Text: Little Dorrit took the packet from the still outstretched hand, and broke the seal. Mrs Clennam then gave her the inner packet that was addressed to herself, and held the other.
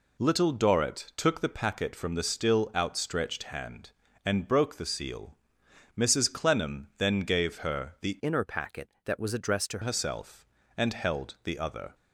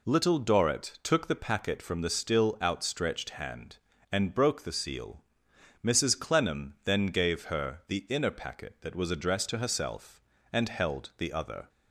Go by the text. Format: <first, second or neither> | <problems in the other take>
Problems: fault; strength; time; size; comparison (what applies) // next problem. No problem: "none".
second | changes voice from "inner" to "to"; from 8.2 to 9.7 s; 1.5 s long